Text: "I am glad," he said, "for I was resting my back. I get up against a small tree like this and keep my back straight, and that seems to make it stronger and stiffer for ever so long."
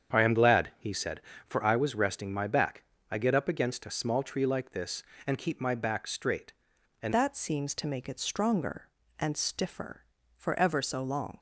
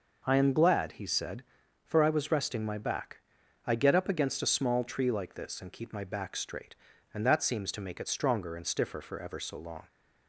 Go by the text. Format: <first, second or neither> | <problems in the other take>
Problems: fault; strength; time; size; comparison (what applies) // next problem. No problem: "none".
second | starts louder than the rest; strong; until 1.2 s; 8 dB // changes voice at "that"; from 7.1 s on; 4.2 s long